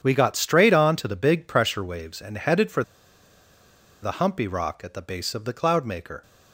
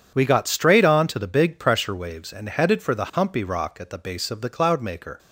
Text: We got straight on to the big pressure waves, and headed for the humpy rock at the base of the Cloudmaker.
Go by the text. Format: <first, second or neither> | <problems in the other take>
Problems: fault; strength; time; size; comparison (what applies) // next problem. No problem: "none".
second | pauses between "for" and "the"; at 2.8 s; 1.2 s long